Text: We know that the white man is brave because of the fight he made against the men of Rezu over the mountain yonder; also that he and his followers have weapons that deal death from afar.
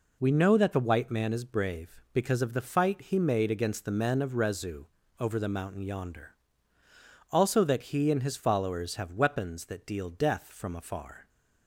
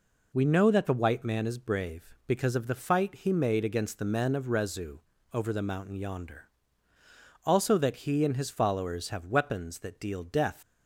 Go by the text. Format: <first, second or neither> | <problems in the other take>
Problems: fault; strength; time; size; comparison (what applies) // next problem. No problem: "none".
first | pauses between "Rezu" and "over"; slight; at 4.9 s; 0.34 s long; slight in the first // stops before "from afar"; at 10.6 s